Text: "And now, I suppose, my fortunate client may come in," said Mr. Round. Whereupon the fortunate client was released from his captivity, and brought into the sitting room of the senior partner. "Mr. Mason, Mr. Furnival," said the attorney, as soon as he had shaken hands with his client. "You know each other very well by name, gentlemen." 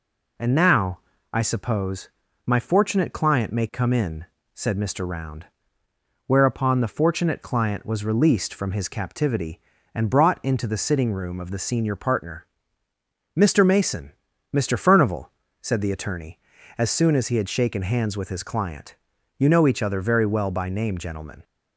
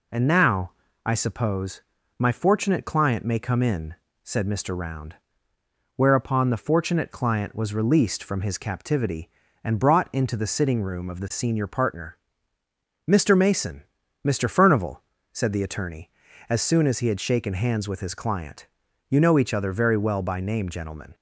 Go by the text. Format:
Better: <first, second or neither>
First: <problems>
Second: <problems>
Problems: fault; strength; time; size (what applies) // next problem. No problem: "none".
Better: neither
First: none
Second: none